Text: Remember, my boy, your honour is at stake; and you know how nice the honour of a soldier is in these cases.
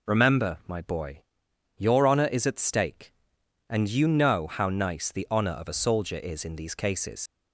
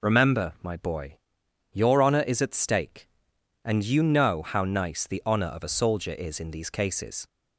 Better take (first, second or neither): second